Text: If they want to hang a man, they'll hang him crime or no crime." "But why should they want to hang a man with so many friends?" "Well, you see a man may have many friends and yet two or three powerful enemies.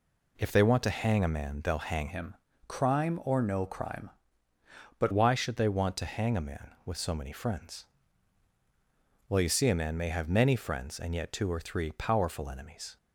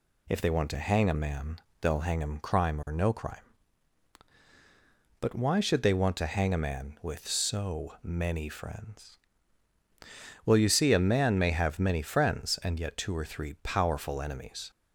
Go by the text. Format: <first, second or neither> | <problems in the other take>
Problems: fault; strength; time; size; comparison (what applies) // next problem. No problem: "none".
second | changes voice from "him" to "But"; from 2.0 to 5.1 s; 3.1 s long // pauses between "him" and "crime"; slight; at 2.3 s; 0.32 s long